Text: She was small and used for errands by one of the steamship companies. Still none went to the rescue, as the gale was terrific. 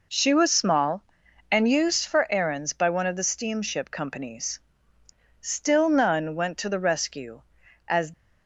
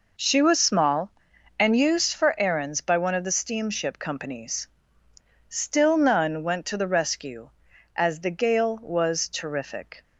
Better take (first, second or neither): second